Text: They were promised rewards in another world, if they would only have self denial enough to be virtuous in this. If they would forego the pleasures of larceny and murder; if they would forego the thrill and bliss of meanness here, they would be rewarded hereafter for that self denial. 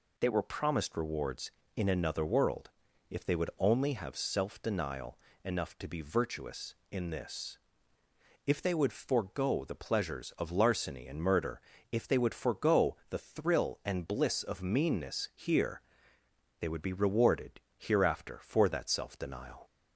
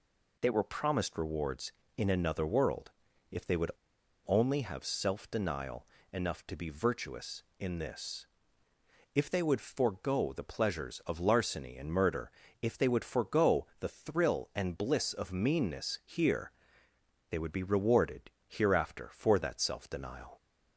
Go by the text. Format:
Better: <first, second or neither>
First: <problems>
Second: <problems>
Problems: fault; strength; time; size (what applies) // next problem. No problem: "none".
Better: first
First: pauses between "denial" and "enough"; slight; at 5.1 s; 0.26 s long // pauses between "rewarded" and "hereafter"; slight; at 17.5 s; 0.18 s long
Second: pauses between "would" and "only"; noticeable; at 3.7 s; 0.55 s long // pauses between "denial" and "enough"; slight; at 5.8 s; 0.26 s long // pauses between "rewarded" and "hereafter"; slight; at 18.2 s; 0.18 s long